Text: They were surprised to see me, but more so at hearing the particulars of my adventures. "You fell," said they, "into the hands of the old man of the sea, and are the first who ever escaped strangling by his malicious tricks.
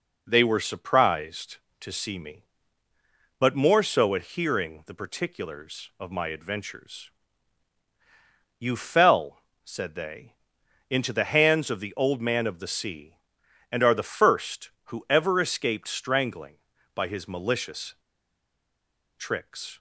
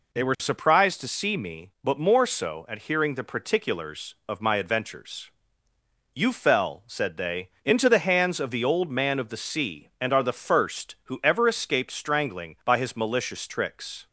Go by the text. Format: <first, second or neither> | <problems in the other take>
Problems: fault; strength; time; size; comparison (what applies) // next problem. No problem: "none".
second | pauses between "malicious" and "tricks"; at 17.9 s; 1.2 s long